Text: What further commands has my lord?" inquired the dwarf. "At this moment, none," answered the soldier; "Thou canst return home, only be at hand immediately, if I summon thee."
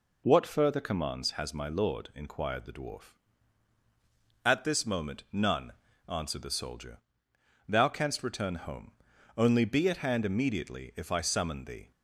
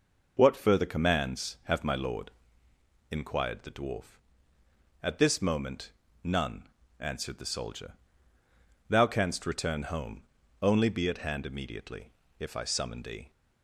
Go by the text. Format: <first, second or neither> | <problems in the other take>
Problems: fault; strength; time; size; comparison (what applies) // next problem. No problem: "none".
first | says "have" for "has"; at 1.6 s